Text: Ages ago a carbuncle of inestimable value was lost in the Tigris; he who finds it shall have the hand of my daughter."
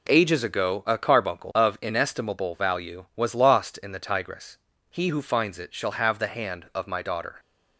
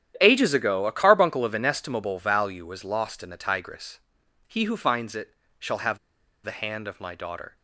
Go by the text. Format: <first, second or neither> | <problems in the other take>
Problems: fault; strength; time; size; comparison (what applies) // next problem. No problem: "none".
first | starts louder than the rest; strong; until 1.2 s; 10.5 dB // pauses between "it" and "shall"; slight; at 5.3 s; 0.26 s long // pauses between "have" and "the"; noticeable; at 5.9 s; 0.46 s long